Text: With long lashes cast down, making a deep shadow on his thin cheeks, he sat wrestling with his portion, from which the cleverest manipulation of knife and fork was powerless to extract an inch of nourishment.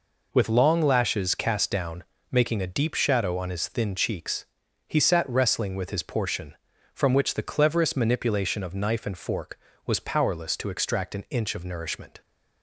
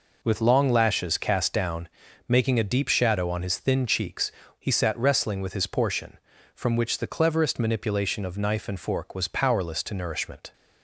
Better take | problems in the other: first | skips "extract an inch of"; at 9.9 s

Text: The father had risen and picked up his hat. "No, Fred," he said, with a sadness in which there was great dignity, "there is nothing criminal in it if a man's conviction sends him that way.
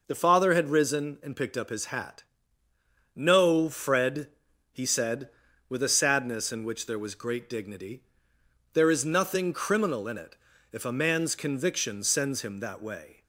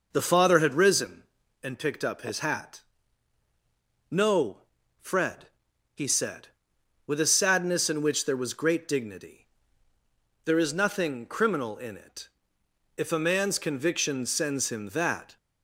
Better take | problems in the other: first | pauses between "it" and "if"; noticeable; at 12.2 s; 0.70 s long; slight in the first // stops before "way"; at 15.3 s

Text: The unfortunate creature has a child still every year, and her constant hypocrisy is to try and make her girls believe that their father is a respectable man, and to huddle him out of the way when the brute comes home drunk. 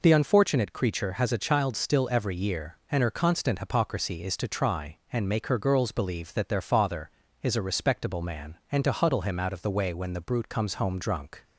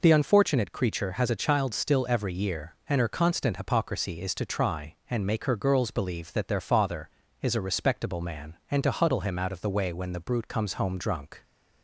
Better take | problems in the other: neither | none

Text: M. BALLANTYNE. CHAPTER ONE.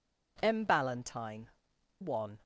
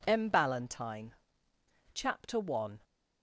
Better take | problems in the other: second | skips "CHAPTER"; at 1.7 s

